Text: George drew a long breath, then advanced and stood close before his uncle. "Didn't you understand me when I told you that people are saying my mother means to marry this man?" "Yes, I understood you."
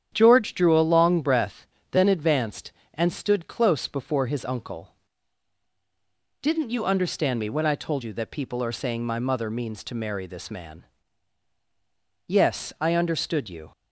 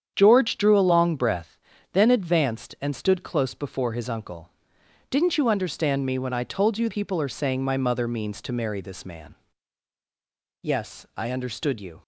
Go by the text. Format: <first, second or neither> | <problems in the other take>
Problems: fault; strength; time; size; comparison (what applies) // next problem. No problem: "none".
first | starts louder than the rest; strong; until 1.1 s; 8.5 dB; strong in the first // skips "that"; at 6.8 s